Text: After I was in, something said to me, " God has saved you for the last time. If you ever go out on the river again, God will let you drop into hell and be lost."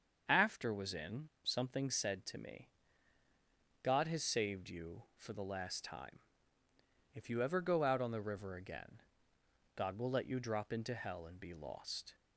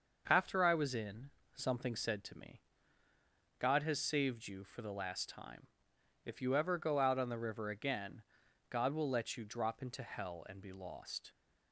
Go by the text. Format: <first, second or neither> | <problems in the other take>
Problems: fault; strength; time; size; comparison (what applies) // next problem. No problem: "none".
second | starts louder than the rest; noticeable; until 1.2 s; 6 dB // skips "I"; at 0.7 s